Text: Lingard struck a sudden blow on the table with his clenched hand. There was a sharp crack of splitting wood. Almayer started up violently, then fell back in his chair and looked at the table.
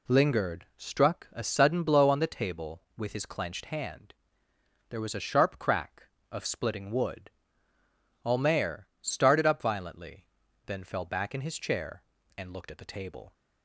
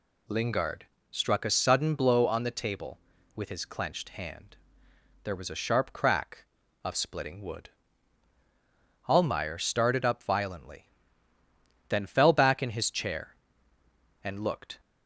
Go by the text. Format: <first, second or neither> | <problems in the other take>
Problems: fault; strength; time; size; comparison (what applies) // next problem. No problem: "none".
first | pauses between "Lingard" and "struck"; slight; at 0.8 s; 0.26 s long // stops before "at the table"; at 14.7 s